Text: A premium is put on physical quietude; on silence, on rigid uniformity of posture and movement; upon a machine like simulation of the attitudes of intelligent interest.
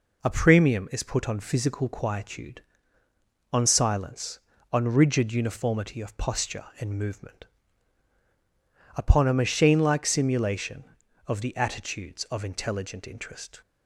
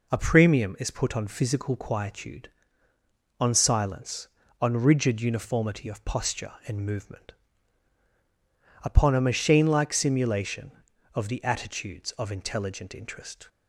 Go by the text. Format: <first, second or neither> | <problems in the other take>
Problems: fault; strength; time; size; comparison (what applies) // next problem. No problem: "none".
neither | none